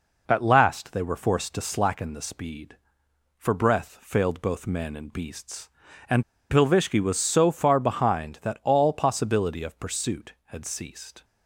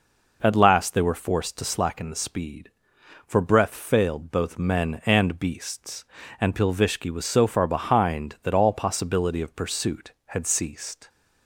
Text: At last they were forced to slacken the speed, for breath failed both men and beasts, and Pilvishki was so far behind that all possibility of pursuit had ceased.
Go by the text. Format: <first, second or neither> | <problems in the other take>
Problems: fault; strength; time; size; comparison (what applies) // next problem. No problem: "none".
second | pauses between "and" and "Pilvishki"; slight; at 6.2 s; 0.27 s long